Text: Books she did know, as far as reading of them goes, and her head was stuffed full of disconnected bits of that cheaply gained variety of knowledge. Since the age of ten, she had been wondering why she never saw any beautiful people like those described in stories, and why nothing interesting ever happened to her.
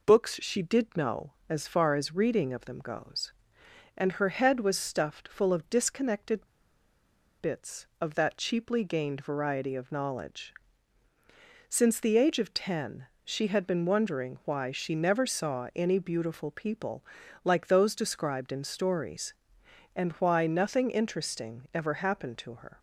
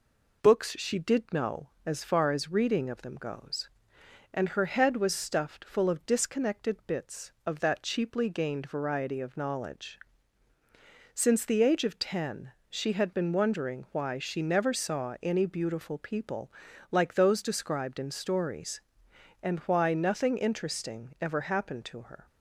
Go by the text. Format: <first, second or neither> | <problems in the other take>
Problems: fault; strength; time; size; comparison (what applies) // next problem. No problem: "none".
second | pauses between "disconnected" and "bits"; at 6.4 s; 0.99 s long // pauses between "people" and "like"; at 17.0 s; 0.40 s long; also in the second